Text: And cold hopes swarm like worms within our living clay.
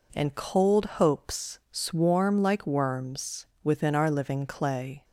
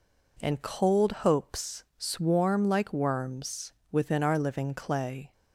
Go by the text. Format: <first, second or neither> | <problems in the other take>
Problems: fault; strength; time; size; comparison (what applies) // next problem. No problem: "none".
neither | pauses between "worms" and "within"; slight; the same in both